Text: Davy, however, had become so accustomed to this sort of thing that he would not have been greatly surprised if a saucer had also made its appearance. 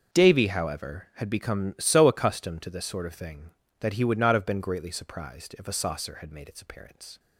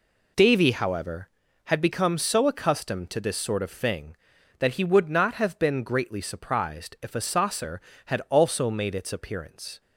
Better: second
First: starts louder than the rest; until 1.2 s; 6.5 dB // skips "also"; at 6.3 s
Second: none

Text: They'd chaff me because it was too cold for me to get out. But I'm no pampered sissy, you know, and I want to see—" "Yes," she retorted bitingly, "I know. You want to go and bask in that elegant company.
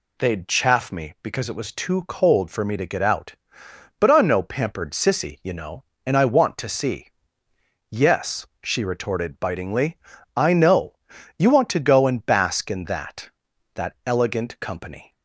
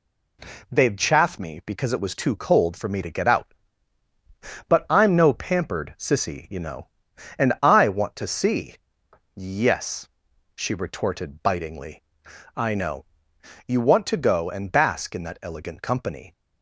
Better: second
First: says "that" twice; at 13.7 s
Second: none

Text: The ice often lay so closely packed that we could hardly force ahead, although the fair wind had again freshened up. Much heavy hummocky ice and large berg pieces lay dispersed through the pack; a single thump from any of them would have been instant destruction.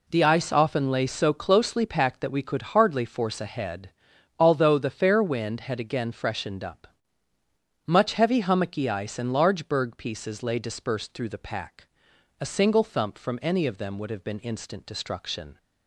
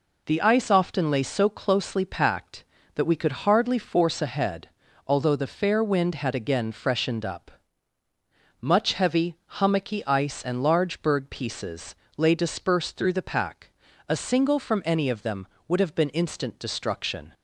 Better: first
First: none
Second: pauses between "heavy" and "hummocky"; slight; at 9.3 s; 0.22 s long // pauses between "pieces" and "lay"; slight; at 11.9 s; 0.22 s long // skips "thump"; at 14.5 s

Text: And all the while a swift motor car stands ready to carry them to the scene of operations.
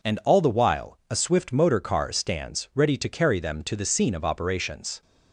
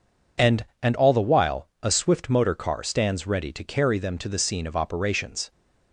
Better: first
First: none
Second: says "And" twice; at 0.8 s // pauses between "while" and "a"; slight; at 1.6 s; 0.16 s long

